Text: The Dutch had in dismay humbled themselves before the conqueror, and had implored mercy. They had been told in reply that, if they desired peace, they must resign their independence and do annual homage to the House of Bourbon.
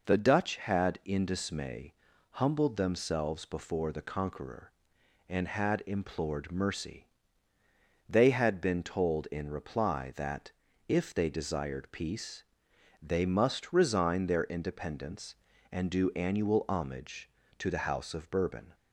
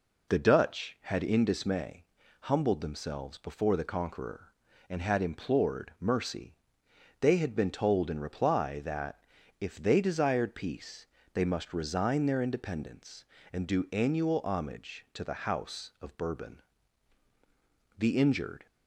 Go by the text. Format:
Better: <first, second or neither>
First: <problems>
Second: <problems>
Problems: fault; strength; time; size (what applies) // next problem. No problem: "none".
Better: first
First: pauses between "dismay" and "humbled"; at 1.9 s; 0.38 s long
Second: pauses between "dismay" and "humbled"; at 2.0 s; 0.38 s long // goes on to say "The injured"; noticeable; from 17.9 s on; 0.68 s long